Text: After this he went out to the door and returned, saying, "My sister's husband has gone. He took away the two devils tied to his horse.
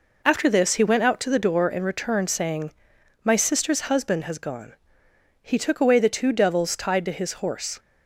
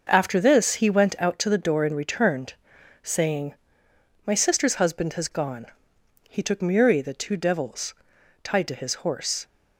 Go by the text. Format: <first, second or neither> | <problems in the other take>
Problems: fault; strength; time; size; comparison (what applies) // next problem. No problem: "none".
first | says "muri" for "away"; at 6.6 s // pauses between "devils" and "tied"; noticeable; at 7.9 s; 0.48 s long